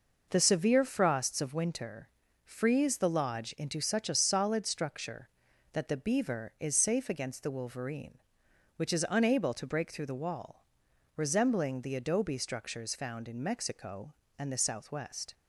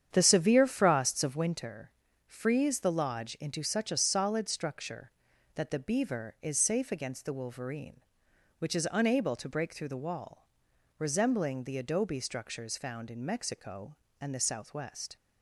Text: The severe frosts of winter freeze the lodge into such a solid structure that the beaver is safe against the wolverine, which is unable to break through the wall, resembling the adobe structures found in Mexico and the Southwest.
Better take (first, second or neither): first